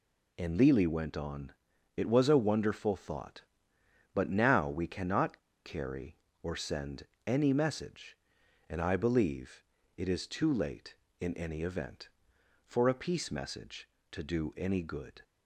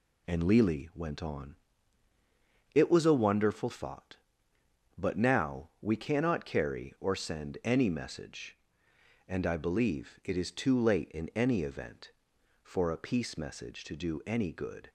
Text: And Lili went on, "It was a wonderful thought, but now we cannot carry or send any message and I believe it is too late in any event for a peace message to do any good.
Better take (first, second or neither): second